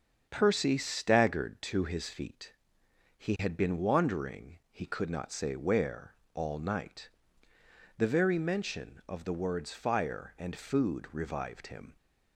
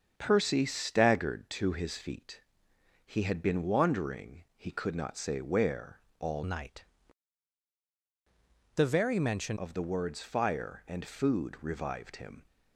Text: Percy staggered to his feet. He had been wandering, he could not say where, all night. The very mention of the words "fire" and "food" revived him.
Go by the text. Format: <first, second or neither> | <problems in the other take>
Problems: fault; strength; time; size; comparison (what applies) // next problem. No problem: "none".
first | starts louder than the rest; strong; until 1.1 s; 7.5 dB; strong in the first // changes voice from "night" to "mention"; from 6.4 to 9.5 s; 3.1 s long